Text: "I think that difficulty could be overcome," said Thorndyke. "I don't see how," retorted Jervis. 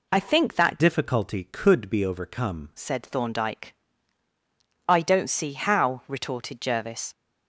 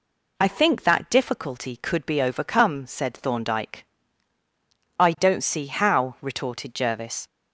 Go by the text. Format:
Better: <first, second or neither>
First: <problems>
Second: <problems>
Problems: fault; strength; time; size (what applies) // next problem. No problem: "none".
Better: second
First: changes voice from "difficulty" to "overcome"; from 0.7 to 2.6 s; 1.9 s long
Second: none